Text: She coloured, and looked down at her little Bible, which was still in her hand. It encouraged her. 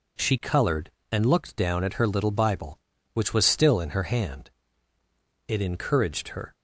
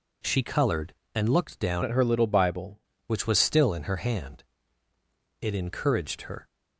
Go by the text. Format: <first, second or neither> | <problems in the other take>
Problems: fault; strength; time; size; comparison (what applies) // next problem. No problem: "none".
first | changes voice from "at" to "Bible"; from 1.8 to 2.8 s; 1.0 s long